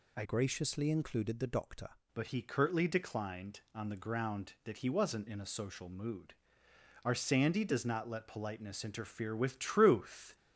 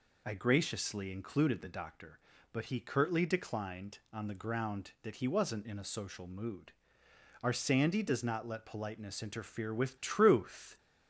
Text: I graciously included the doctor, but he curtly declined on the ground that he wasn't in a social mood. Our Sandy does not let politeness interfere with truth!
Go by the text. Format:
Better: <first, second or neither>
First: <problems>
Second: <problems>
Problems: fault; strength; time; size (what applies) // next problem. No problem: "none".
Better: second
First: changes voice from "graciously" to "doctor"; from 0.2 to 1.8 s; 1.6 s long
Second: none